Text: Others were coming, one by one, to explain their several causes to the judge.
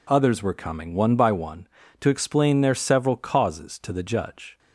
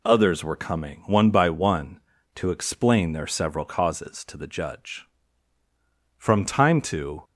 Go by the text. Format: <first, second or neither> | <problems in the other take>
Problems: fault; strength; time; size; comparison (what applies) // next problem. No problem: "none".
first | goes on to say "From time to"; noticeable; from 6.1 s on; 1.0 s long